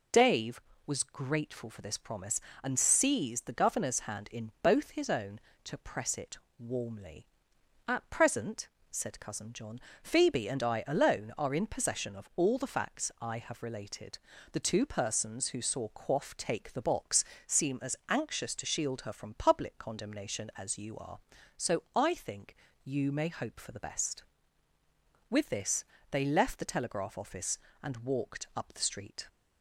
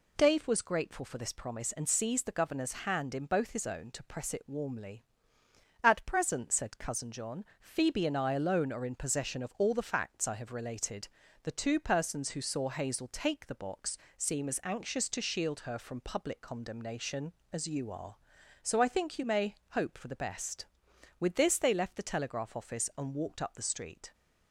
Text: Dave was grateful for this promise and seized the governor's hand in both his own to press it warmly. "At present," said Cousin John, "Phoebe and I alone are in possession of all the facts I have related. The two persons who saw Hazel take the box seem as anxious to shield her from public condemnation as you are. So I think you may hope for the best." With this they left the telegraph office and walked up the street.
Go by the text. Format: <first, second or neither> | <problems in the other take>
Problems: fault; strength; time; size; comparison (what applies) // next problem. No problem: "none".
second | pauses between "it" and "warmly"; slight; at 6.3 s; 0.20 s long // says "Quaff" for "Hazel"; at 15.8 s // pauses between "box" and "seem"; slight; at 17.2 s; 0.24 s long; slight in the second // pauses between "think" and "you"; slight; at 22.5 s; 0.30 s long // pauses between "this" and "they"; slight; at 25.8 s; 0.28 s long